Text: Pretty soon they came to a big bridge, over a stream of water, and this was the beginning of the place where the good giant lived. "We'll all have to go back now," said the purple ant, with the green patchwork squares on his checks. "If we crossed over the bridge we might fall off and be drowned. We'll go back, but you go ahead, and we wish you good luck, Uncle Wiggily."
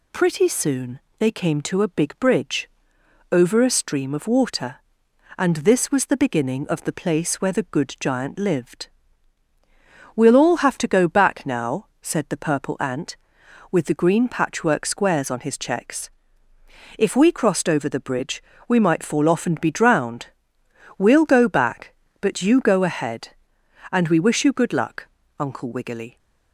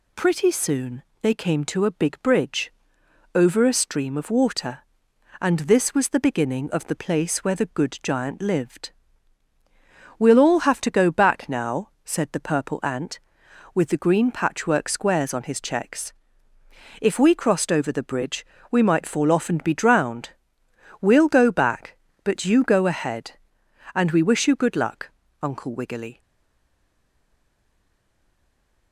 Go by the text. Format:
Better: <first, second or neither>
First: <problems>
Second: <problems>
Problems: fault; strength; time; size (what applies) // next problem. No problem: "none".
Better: first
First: pauses between "soon" and "they"; slight; at 1.0 s; 0.18 s long // pauses between "bridge" and "we"; slight; at 18.4 s; 0.24 s long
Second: pauses between "soon" and "they"; slight; at 1.0 s; 0.18 s long // pauses between "bridge" and "we"; slight; at 18.4 s; 0.24 s long // stays silent after the last word; strong; from 26.2 s on; 2.7 s long